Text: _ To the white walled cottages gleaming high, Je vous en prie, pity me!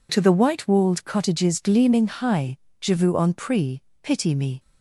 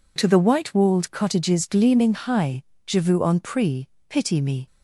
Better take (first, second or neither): neither